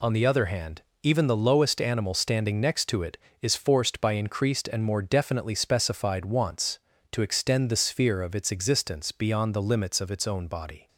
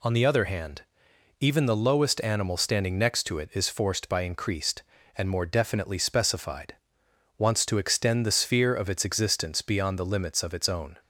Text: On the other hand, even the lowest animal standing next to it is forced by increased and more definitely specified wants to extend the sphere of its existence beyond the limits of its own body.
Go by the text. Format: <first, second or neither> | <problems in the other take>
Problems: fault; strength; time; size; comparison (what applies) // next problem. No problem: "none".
first | pauses between "specified" and "wants"; noticeable; at 6.7 s; 0.64 s long // stops before "body"; at 11.0 s